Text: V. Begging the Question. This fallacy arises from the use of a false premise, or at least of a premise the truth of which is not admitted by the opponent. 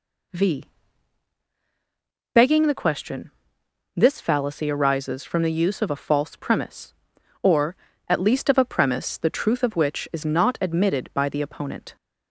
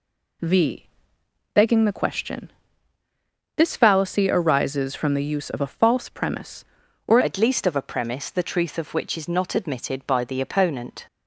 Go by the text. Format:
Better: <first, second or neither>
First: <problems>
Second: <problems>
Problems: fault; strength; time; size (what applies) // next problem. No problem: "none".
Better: first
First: none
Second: changes voice at "at"; from 7.2 s on; 3.8 s long